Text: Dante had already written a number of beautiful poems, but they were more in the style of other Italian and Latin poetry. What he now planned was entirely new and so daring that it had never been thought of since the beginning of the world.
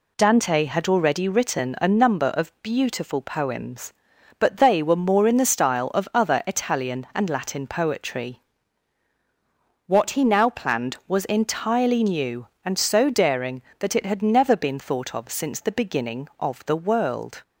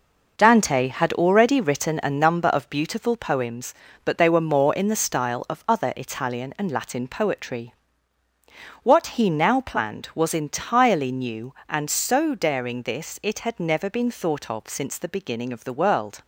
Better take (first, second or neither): first